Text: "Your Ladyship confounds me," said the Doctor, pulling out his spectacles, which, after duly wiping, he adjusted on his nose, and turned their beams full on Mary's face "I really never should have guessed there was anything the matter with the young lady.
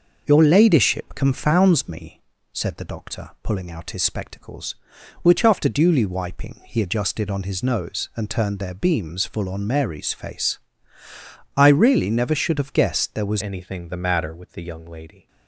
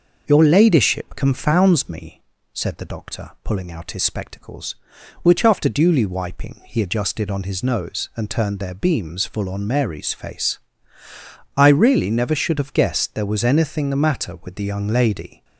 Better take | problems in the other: second | pauses between "face" and "I"; noticeable; at 10.5 s; 0.98 s long; noticeable in the second // changes voice at "anything"; from 13.4 s on; 1.8 s long

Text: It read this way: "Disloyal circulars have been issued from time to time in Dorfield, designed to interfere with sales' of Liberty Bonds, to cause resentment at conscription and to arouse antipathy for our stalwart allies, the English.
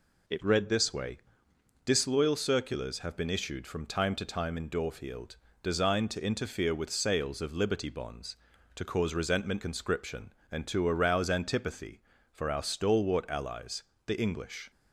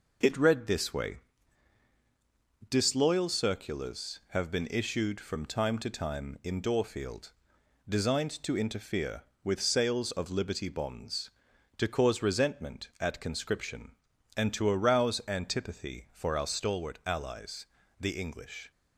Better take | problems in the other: second | skips "at"; at 9.6 s

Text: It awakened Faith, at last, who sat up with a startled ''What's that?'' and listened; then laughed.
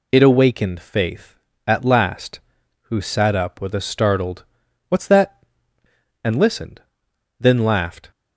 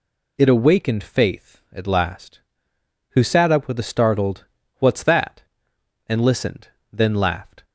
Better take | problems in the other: neither | pauses between "startled" and "What's"; the same in both

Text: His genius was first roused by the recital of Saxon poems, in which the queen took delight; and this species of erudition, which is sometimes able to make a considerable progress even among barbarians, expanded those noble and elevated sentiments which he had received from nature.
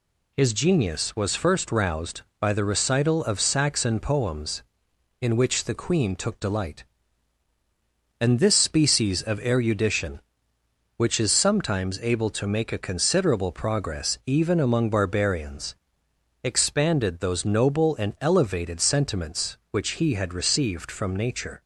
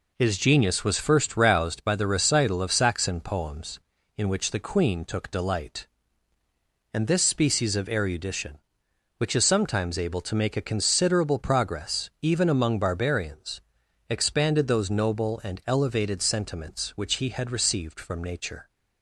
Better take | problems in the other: neither | none

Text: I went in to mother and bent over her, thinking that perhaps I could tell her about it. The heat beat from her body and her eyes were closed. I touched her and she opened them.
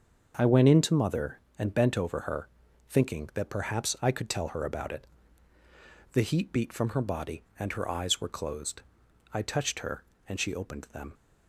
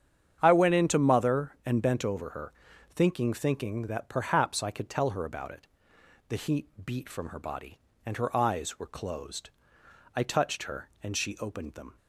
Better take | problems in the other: first | starts louder than the rest; strong; until 1.4 s; 8.5 dB; also in the first // says "thinking" twice; at 3.3 s // pauses between "heat" and "beat"; slight; at 6.6 s; 0.18 s long

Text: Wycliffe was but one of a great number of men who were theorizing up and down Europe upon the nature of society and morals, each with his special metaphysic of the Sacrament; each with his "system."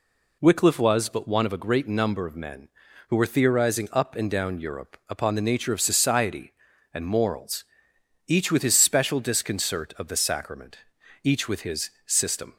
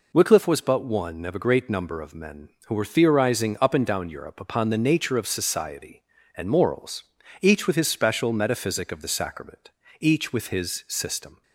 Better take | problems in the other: second | says "disconcert" for "metaphysic"; at 9.2 s // pauses between "his" and "system"; slight; at 11.8 s; 0.16 s long

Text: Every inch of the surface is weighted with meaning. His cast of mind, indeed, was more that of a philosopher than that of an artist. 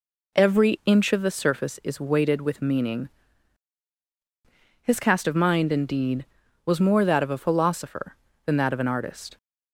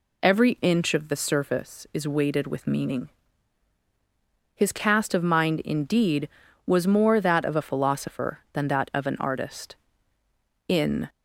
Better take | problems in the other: first | goes on to say "In"; slight; from 10.6 s on; 0.40 s long

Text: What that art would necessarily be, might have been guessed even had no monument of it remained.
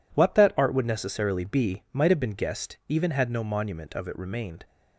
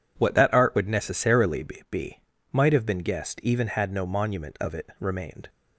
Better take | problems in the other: first | says "be" twice; at 1.9 s

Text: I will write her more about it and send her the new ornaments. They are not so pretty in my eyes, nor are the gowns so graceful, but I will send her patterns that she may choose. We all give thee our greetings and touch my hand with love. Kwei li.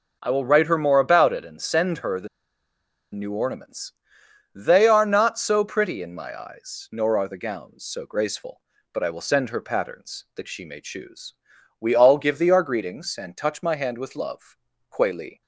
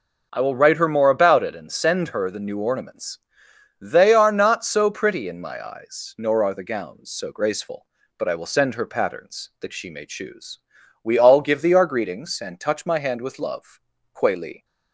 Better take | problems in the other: second | pauses between "the" and "new"; noticeable; at 2.2 s; 0.85 s long

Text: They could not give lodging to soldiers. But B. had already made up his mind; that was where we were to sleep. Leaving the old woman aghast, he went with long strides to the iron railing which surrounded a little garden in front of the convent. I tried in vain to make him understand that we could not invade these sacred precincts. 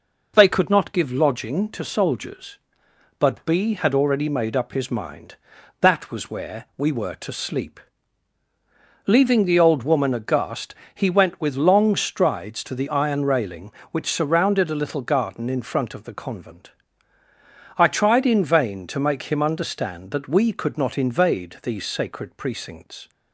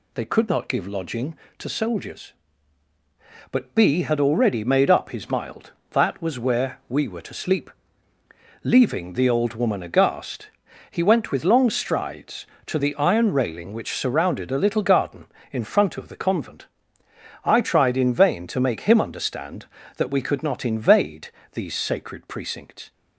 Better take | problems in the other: first | says "mild" for "mind"; at 5.2 s // pauses between "invade" and "these"; slight; at 21.3 s; 0.22 s long

